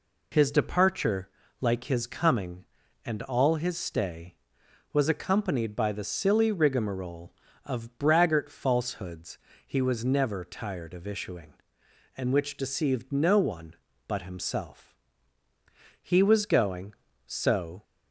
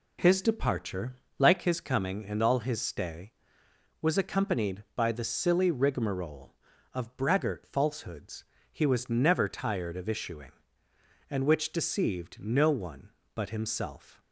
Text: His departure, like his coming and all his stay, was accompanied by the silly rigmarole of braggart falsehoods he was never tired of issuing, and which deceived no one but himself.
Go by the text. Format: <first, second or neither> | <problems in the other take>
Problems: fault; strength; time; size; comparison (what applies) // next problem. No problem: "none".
second | pauses between "falsehoods" and "he"; slight; at 9.3 s; 0.30 s long; slight in the second // goes on to say "He was going so"; strong; from 16.0 s on; 1.8 s long